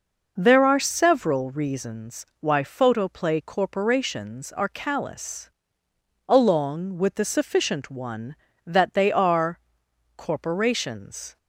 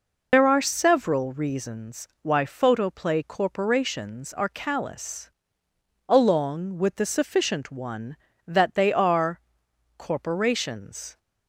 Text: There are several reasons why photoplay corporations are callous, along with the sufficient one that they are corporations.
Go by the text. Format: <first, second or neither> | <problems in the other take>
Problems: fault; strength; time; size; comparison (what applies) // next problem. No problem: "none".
first | loses the start of "There"; at 0.3 s; 135 ms // pauses between "are" and "corporations"; noticeable; at 9.3 s; 0.60 s long; noticeable in the first